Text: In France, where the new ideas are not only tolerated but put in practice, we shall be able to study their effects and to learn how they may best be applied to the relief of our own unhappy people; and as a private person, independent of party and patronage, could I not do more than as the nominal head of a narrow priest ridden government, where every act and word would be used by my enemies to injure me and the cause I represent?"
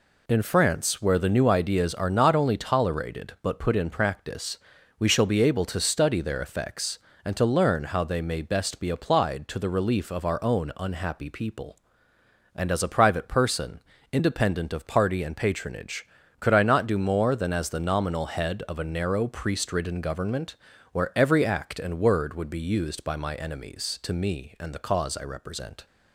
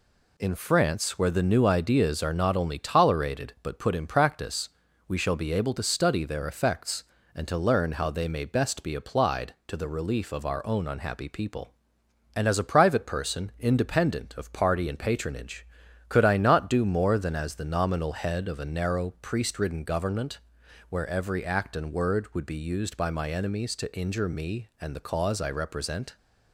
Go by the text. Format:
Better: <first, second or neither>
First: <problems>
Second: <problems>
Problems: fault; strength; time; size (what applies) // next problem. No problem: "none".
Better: second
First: skips "injure"; at 24.1 s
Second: none